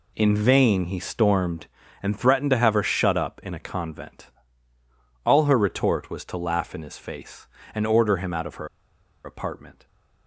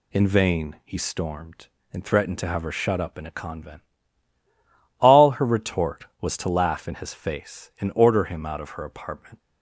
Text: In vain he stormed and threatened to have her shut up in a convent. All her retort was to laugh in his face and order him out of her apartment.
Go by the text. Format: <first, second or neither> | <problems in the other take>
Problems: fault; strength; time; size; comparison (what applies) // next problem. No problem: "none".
second | pauses between "her" and "apartment"; noticeable; at 8.6 s; 0.57 s long